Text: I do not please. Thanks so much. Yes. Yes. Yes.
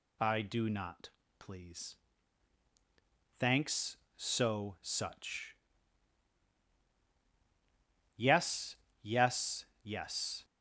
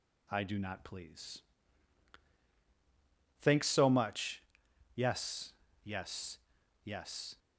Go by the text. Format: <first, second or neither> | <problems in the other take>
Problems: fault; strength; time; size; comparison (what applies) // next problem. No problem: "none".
second | pauses between "not" and "please"; slight; at 1.1 s; 0.28 s long // says "such" for "much"; at 4.8 s